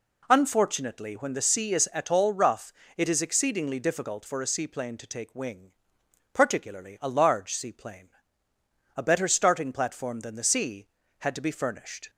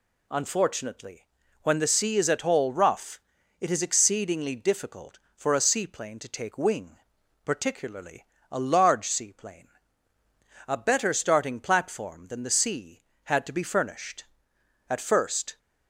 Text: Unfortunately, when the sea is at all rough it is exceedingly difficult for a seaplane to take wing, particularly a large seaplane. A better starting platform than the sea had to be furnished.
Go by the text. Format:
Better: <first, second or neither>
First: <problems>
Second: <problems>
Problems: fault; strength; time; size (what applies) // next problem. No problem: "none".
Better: first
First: pauses between "rough" and "it"; slight; at 2.7 s; 0.24 s long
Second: pauses between "rough" and "it"; at 3.2 s; 0.40 s long // pauses between "particularly" and "a"; slight; at 8.2 s; 0.28 s long // goes on to say "At first"; noticeable; from 14.9 s on; 0.68 s long